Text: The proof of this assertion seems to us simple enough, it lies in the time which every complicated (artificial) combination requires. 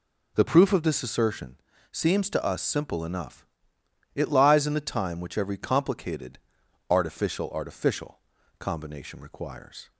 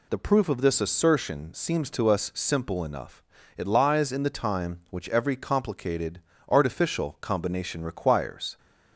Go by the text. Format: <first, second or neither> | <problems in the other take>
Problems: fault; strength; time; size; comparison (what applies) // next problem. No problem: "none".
second | pauses between "assertion" and "seems"; slight; at 1.5 s; 0.34 s long // says "artificial" twice; at 7.4 s